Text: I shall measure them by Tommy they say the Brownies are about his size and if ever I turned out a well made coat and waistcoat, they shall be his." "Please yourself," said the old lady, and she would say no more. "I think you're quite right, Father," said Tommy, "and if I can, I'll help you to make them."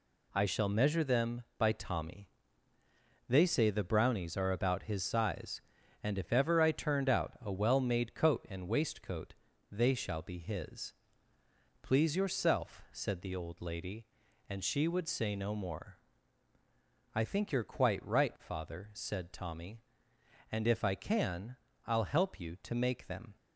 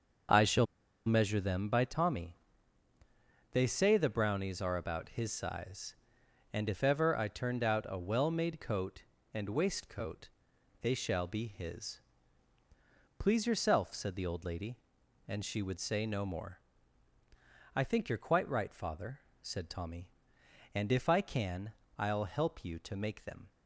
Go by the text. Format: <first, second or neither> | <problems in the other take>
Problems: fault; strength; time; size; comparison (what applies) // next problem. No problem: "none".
first | starts louder than the rest; noticeable; until 1.7 s; 6 dB // pauses between "shall" and "measure"; at 0.6 s; 0.40 s long // pauses between "Tommy" and "they"; at 2.3 s; 1.1 s long; also in the first